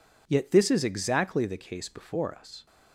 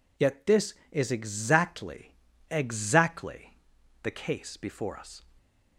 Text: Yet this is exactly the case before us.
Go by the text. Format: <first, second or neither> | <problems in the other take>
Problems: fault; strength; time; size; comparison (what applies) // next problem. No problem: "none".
first | says "exactly" twice; at 2.5 s